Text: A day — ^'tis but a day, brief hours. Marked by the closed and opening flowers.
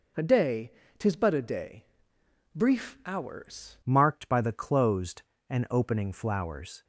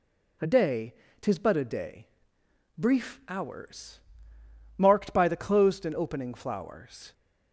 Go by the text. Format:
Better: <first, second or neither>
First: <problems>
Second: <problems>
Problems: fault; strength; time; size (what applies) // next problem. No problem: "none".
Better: second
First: changes voice at "Marked"; from 3.8 s on; 3.0 s long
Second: none